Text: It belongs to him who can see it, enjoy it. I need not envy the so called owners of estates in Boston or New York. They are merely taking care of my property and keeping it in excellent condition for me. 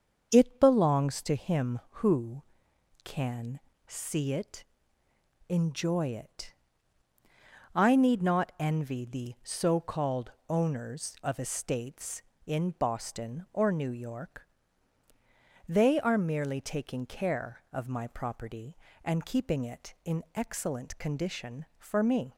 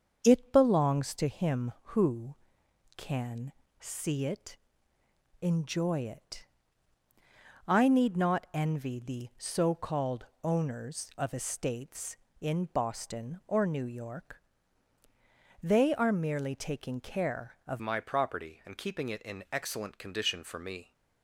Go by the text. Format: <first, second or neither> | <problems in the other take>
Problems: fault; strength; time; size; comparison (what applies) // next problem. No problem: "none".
first | starts louder than the rest; until 1.2 s; 7 dB; also in the first // pauses between "can" and "see"; slight; at 3.5 s; 0.26 s long; slight in the first // pauses between "called" and "owners"; slight; at 10.2 s; 0.18 s long; slight in the first // changes voice at "my"; from 17.7 s on; 3.2 s long